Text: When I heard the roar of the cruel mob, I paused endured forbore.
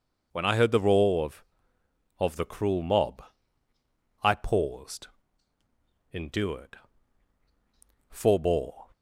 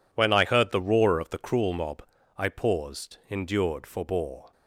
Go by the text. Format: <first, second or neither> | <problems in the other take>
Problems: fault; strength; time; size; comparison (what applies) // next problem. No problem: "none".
second | says "of" twice; at 2.2 s // pauses between "paused" and "endured"; at 5.0 s; 1.0 s long // pauses between "endured" and "forbore"; strong; at 6.7 s; 1.3 s long